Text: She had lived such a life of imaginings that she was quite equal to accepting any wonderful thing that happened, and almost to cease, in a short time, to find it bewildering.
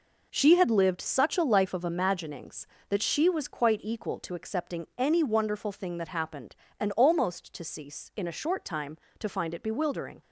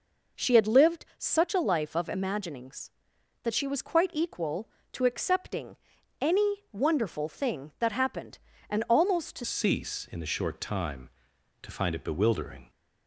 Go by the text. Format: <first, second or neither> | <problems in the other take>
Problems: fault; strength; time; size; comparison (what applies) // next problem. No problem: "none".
first | pauses between "accepting" and "any"; at 5.7 s; 0.44 s long // changes voice at "cease"; from 9.4 s on; 3.2 s long